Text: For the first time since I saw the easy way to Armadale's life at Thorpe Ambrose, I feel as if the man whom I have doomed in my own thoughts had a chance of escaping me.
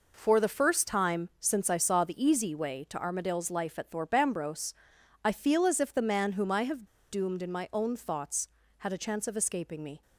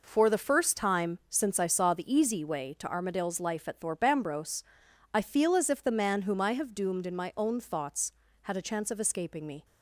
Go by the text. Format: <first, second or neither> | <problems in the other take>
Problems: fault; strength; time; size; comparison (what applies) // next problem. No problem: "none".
second | pauses between "have" and "doomed"; slight; at 6.8 s; 0.27 s long